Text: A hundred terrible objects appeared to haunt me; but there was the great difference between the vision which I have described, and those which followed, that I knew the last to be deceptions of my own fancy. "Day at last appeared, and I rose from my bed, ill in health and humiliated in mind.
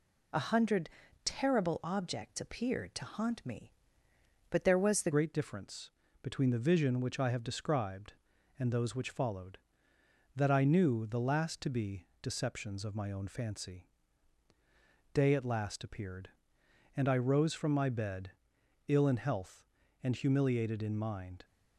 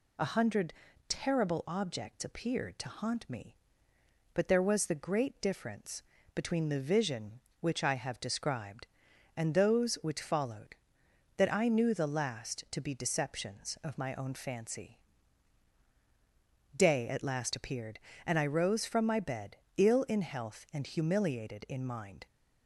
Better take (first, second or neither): second